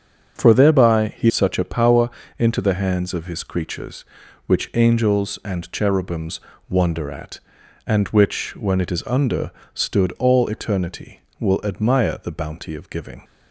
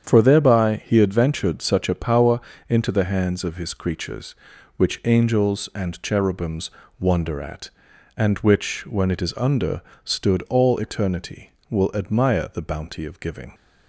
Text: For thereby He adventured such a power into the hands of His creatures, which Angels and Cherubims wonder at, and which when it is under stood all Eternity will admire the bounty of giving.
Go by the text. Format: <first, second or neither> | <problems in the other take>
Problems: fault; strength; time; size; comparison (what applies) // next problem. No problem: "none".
second | starts louder than the rest; until 1.4 s; 7 dB; strong in the second // skips "adventured"; at 1.3 s // pauses between "power" and "into"; slight; at 2.0 s; 0.30 s long; slight in the second // pauses between "Cherubims" and "wonder"; slight; at 6.3 s; 0.30 s long; slight in the second // pauses between "under" and "stood"; slight; at 9.4 s; 0.24 s long; slight in the second